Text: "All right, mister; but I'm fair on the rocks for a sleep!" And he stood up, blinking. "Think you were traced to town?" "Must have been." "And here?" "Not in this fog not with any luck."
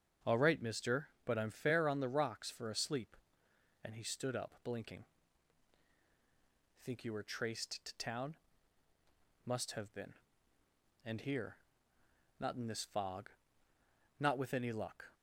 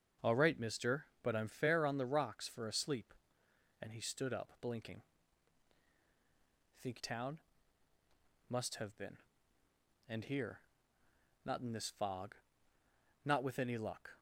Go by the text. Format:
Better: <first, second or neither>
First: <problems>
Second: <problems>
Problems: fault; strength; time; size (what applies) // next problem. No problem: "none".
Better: first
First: starts louder than the rest; until 1.4 s; 7 dB // pauses between "fog" and "not"; noticeable; at 13.2 s; 0.90 s long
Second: starts louder than the rest; until 1.3 s; 7 dB // skips "you were traced to"; at 7.0 s // pauses between "fog" and "not"; noticeable; at 12.3 s; 0.90 s long